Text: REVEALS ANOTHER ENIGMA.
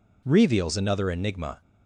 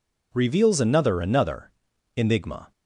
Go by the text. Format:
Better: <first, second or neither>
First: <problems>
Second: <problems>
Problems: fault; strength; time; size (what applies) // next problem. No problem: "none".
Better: first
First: none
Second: says "ANOTHER" twice; at 1.1 s